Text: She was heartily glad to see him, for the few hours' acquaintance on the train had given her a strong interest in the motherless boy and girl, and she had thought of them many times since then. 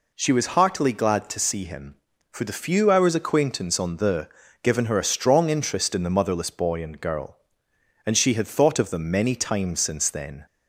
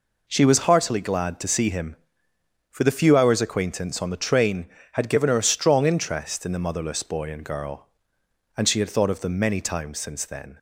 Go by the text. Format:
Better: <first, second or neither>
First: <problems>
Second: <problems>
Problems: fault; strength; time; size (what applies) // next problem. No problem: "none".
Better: second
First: skips "train had"; at 4.4 s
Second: none